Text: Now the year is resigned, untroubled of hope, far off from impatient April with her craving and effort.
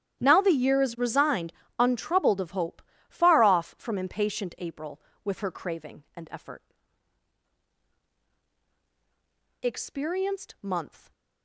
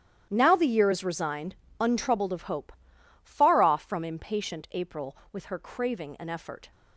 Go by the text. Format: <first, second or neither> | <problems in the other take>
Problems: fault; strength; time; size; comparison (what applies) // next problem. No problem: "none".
second | starts louder than the rest; strong; until 1.2 s; 11 dB; strong in the second // goes on to say "Experienced month"; from 9.6 s on; 1.5 s long